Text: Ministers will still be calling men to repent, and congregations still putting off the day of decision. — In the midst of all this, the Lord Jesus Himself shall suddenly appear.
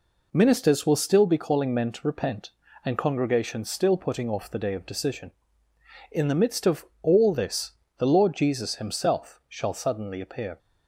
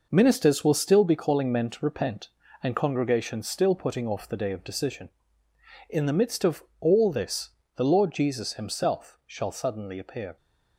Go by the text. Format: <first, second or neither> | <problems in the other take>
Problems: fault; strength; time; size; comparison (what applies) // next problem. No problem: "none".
first | gets quieter; strong; throughout; 7.5 dB // pauses between "of" and "all"; slight; at 6.6 s; 0.18 s long; slight in the first